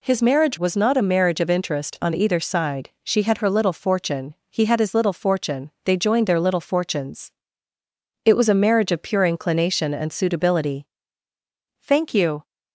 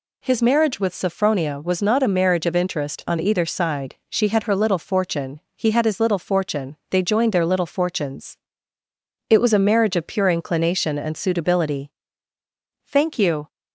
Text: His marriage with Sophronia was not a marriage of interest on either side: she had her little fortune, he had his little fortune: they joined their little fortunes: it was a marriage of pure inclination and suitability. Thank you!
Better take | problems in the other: second | skips "with Sophronia"; at 0.5 s

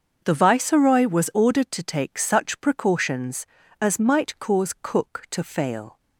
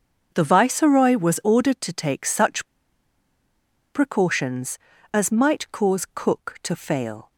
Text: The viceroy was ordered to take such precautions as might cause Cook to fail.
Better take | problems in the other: first | starts louder than the rest; until 1.3 s; 6.5 dB; also in the first // pauses between "such" and "precautions"; strong; at 2.6 s; 1.2 s long

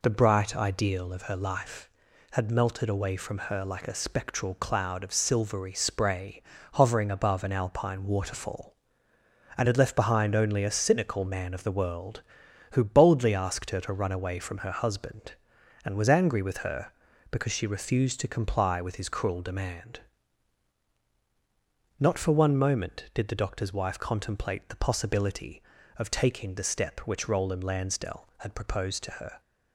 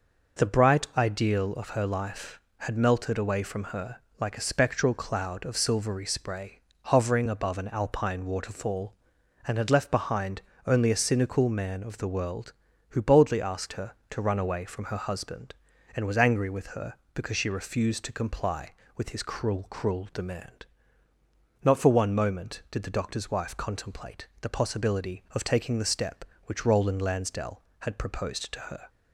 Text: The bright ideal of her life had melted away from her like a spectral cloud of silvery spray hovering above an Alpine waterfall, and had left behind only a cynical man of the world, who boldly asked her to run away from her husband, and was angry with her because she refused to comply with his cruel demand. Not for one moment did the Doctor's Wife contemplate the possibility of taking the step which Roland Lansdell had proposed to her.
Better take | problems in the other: first | pauses between "her" and "like"; slight; at 3.9 s; 0.22 s long // pauses between "spray" and "hovering"; slight; at 6.5 s; 0.34 s long; slight in the first // pauses between "behind" and "only"; slight; at 10.4 s; 0.24 s long // says "cruel" twice; at 19.7 s // pauses between "contemplate" and "the"; slight; at 24.2 s; 0.16 s long

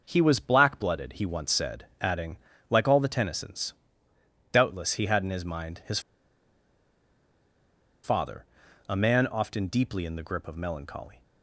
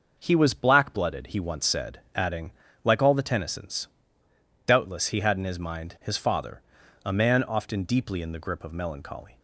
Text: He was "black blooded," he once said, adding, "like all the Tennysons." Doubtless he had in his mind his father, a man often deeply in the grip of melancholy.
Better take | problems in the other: second | pauses between "his" and "father"; strong; at 5.9 s; 2.0 s long

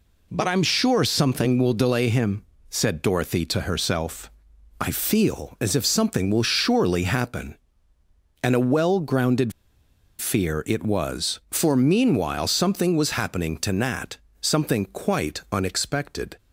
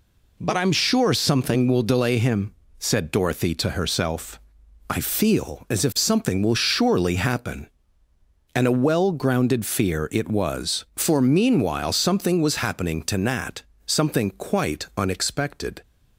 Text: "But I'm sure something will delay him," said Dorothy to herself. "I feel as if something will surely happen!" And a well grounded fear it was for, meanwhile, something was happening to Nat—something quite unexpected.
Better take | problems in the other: second | pauses between "grounded" and "fear"; noticeable; at 9.5 s; 0.69 s long

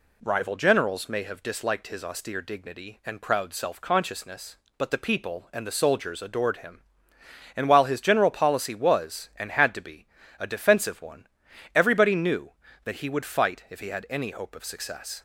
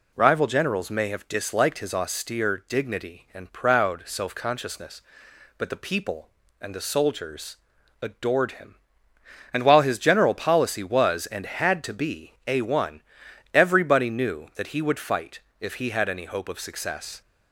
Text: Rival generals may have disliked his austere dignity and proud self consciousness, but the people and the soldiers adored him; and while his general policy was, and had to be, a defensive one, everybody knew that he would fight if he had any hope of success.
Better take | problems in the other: first | pauses between "soldiers" and "adored"; noticeable; at 7.5 s; 0.46 s long // skips "defensive"; at 12.6 s // pauses between "fight" and "if"; slight; at 15.3 s; 0.22 s long

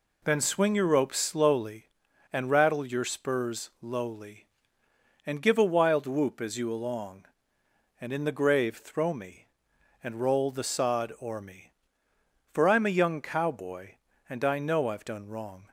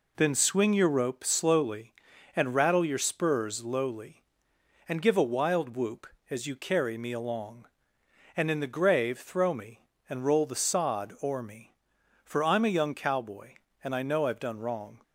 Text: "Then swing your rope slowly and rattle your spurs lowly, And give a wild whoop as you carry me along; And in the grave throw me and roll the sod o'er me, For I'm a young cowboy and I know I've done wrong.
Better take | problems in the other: second | skips "carry me"; at 6.7 s

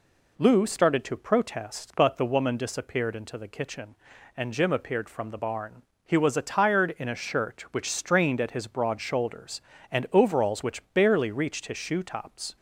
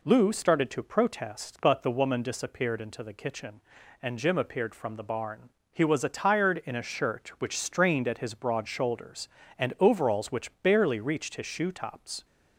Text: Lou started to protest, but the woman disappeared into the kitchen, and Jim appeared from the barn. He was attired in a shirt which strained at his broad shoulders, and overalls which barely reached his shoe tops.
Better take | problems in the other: neither | none

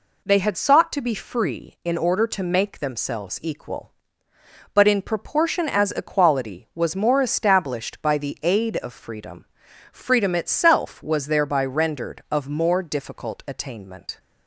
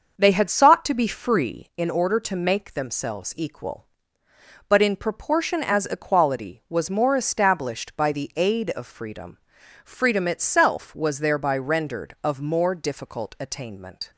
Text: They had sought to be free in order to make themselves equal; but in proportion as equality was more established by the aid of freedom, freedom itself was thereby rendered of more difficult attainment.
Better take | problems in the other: first | starts louder than the rest; until 1.8 s; 6.5 dB

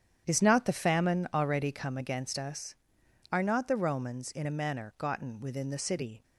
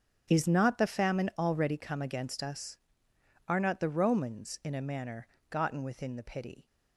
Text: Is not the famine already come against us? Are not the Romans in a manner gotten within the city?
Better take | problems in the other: first | starts louder than the rest; strong; until 1.3 s; 9 dB; strong in the first // pauses between "manner" and "gotten"; slight; at 5.2 s; 0.22 s long // says "pity" for "city"; at 6.2 s

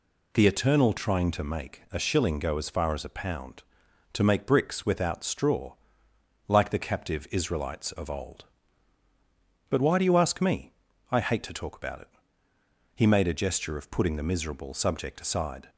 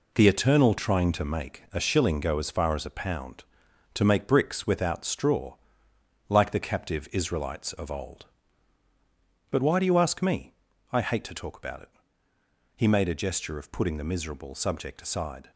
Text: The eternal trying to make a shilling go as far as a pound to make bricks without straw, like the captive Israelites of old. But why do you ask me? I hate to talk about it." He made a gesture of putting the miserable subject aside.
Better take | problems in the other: first | gets quieter; strong; throughout; 8 dB

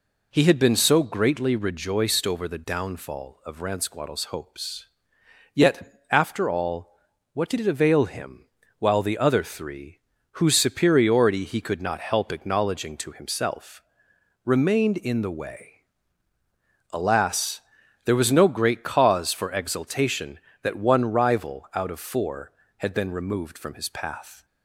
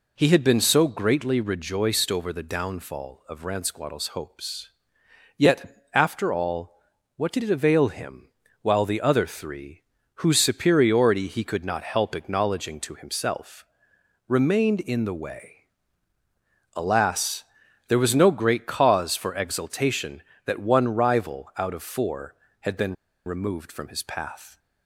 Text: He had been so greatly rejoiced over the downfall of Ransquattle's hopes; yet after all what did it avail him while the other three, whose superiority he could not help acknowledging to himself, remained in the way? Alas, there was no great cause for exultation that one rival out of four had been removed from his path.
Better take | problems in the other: first | pauses between "all" and "what"; at 6.7 s; 0.38 s long; also in the first // pauses between "him" and "while"; slight; at 8.2 s; 0.32 s long; slight in the first // pauses between "been" and "removed"; slight; at 22.9 s; 0.32 s long

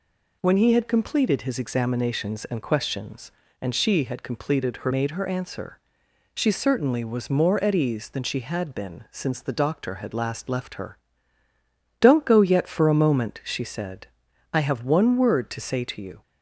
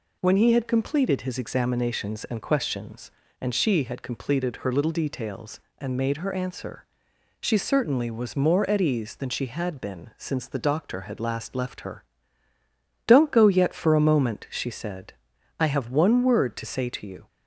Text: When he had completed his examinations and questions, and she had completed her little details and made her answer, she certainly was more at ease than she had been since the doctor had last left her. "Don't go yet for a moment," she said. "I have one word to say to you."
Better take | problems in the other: second | skips "little details and"; at 4.9 s

